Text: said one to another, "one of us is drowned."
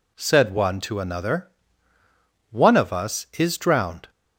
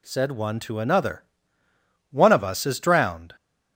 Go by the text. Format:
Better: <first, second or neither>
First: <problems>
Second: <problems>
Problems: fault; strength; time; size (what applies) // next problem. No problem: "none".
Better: neither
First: none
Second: none